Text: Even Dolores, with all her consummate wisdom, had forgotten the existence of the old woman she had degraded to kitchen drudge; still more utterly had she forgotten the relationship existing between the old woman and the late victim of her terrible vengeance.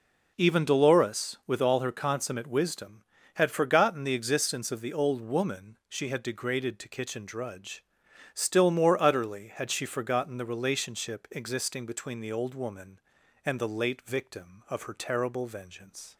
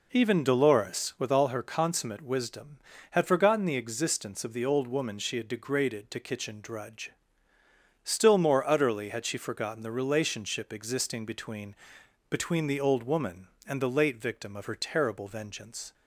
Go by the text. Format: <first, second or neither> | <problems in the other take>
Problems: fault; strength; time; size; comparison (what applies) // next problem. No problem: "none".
first | says "between" twice; at 12.3 s